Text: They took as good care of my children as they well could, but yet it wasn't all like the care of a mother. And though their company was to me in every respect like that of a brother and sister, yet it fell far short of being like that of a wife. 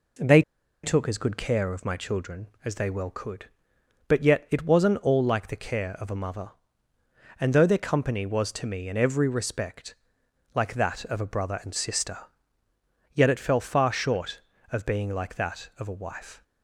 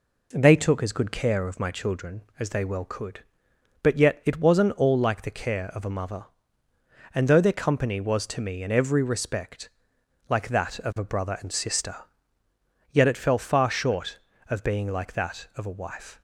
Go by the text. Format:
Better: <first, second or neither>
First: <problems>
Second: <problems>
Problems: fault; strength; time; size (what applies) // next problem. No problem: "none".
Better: second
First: pauses between "They" and "took"; at 0.4 s; 0.42 s long // pauses between "respect" and "like"; noticeable; at 9.9 s; 0.62 s long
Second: pauses between "respect" and "like"; noticeable; at 9.6 s; 0.62 s long